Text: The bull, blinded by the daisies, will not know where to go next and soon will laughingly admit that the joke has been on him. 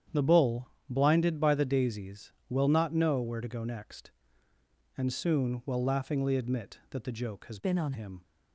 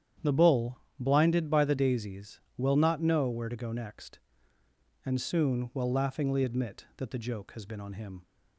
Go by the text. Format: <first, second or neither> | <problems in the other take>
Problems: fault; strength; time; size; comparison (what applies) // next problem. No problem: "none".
second | starts louder than the rest; strong; until 1.3 s; 9 dB; strong in the second // changes voice from "been" to "on"; from 7.5 to 7.9 s; 0.4 s long